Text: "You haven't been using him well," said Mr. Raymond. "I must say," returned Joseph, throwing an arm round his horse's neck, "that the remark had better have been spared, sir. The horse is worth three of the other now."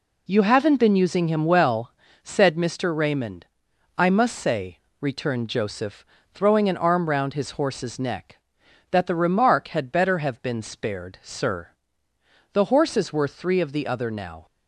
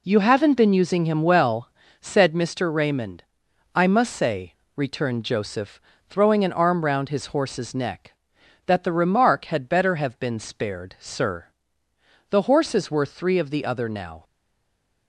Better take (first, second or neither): first